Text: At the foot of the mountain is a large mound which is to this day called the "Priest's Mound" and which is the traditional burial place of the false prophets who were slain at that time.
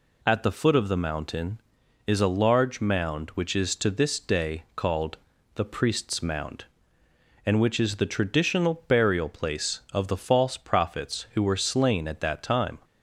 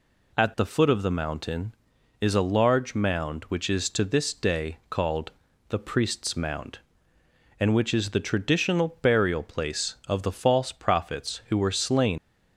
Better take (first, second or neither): first